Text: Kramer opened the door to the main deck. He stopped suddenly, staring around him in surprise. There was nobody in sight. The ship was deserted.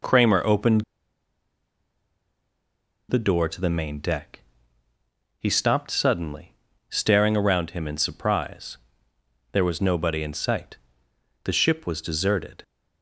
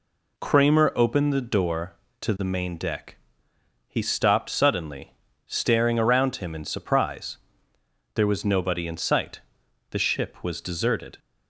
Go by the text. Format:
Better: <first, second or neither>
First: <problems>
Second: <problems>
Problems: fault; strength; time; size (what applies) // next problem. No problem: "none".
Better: second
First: pauses between "opened" and "the"; strong; at 0.8 s; 2.2 s long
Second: none